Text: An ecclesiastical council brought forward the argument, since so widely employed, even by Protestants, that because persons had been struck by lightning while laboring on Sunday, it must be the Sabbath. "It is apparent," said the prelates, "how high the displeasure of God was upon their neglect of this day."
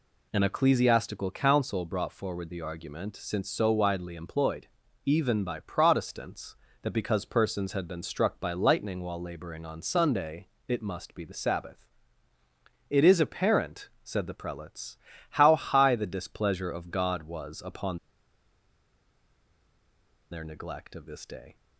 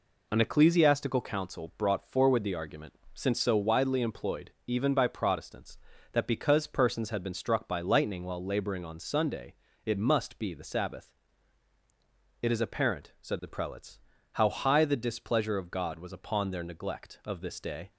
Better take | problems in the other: second | pauses between "upon" and "their"; strong; at 17.9 s; 2.3 s long

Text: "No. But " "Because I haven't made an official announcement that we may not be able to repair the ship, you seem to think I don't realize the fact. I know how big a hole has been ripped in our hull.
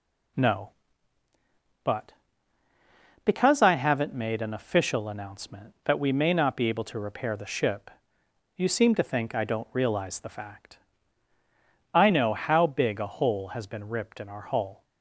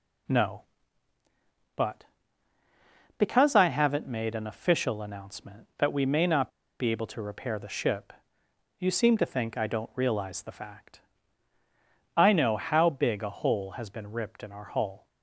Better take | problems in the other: first | pauses between "not" and "be"; slight; at 6.4 s; 0.30 s long

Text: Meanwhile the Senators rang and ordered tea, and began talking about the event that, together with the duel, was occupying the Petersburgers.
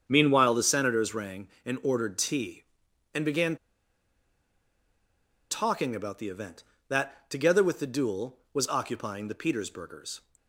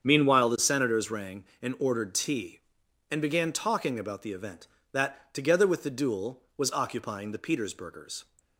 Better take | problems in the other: second | starts louder than the rest; strong; until 1.0 s; 8 dB; strong in the second // pauses between "began" and "talking"; strong; at 3.5 s; 1.9 s long

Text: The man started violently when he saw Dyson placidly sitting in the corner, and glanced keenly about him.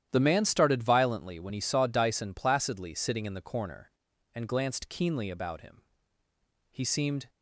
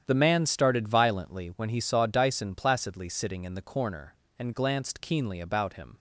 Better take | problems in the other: second | starts louder than the rest; strong; until 1.1 s; 11 dB; strong in the second // goes on to say "He seemed"; from 6.7 s on; 0.58 s long

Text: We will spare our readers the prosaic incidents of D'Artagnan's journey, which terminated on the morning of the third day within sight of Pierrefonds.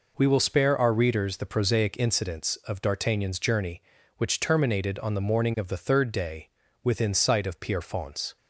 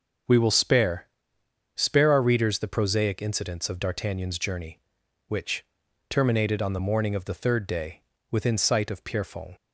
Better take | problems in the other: first | says "spare" twice; at 1.7 s // pauses between "which" and "terminated"; at 5.6 s; 0.42 s long // pauses between "day" and "within"; slight; at 8.0 s; 0.28 s long; slight in the first

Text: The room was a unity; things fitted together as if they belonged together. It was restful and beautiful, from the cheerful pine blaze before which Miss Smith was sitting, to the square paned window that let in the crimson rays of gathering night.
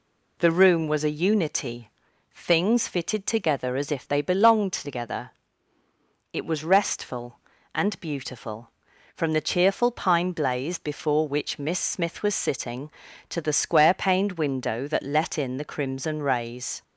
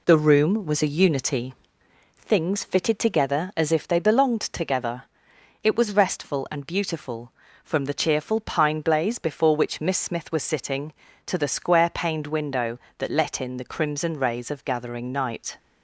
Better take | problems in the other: second | stops before "of gathering night"; at 16.8 s

